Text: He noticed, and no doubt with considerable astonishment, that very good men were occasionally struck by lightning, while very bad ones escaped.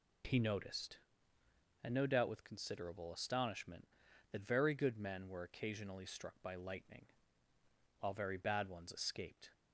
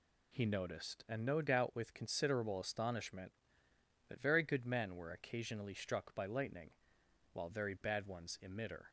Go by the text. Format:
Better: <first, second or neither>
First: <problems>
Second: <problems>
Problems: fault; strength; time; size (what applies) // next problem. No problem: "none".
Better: first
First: none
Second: says "emitter" for "escaped"; at 8.4 s